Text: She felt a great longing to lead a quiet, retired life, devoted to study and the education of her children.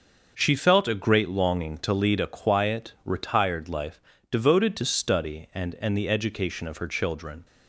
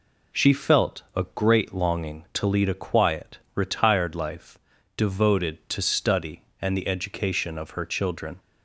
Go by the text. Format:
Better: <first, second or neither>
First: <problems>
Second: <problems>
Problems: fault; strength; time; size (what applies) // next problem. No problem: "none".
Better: second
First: starts louder than the rest; until 1.3 s; 6.5 dB // says "and" twice; at 5.7 s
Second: none